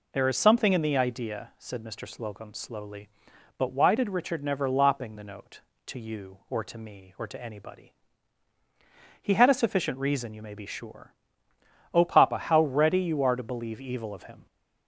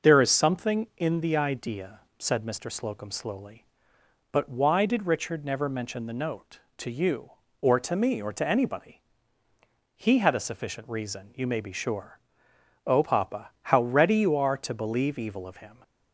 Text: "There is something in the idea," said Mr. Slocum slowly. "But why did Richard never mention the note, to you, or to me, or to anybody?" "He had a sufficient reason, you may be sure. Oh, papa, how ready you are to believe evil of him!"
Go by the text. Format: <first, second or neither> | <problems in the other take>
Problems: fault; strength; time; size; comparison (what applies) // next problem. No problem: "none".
second | says "lopping" for "mention"; at 4.6 s